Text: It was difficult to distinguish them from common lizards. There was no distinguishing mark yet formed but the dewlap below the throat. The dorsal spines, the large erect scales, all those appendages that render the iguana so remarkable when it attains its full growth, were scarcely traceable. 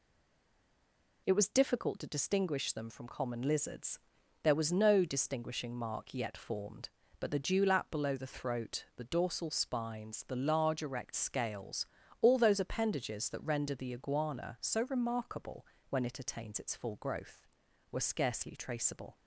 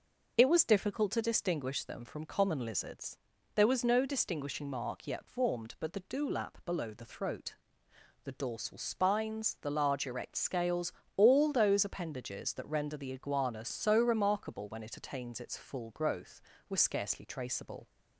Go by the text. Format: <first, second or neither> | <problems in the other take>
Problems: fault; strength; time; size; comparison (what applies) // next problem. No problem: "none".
second | stays silent before the first word; noticeable; until 1.2 s; 1.2 s long // pauses between "remarkable" and "when"; slight; at 15.6 s; 0.24 s long